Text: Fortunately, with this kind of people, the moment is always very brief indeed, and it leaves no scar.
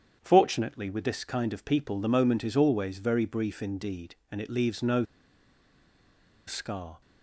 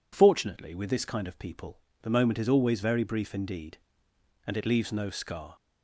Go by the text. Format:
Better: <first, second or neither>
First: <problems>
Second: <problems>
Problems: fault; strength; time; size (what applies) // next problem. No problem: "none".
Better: second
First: starts louder than the rest; strong; until 1.2 s; 9 dB // pauses between "no" and "scar"; strong; at 5.0 s; 1.4 s long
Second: none